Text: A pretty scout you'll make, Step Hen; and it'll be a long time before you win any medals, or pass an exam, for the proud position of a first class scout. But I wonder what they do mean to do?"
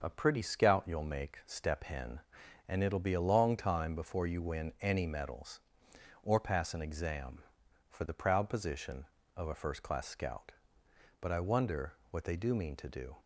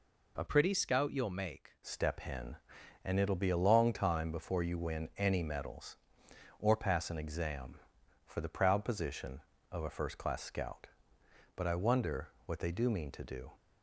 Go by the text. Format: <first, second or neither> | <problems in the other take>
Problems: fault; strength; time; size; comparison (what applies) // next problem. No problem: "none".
first | changes voice from "pretty" to "make"; from 0.4 to 1.7 s; 1.3 s long // pauses between "wonder" and "what"; slight; at 12.2 s; 0.18 s long; slight in the first